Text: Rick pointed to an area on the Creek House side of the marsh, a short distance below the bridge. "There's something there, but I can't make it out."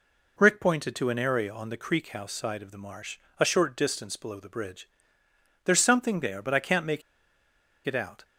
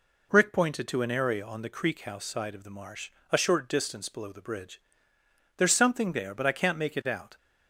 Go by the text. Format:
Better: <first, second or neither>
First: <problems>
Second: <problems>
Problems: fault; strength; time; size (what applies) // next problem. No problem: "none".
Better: second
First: pauses between "make" and "it"; noticeable; at 7.0 s; 0.84 s long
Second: none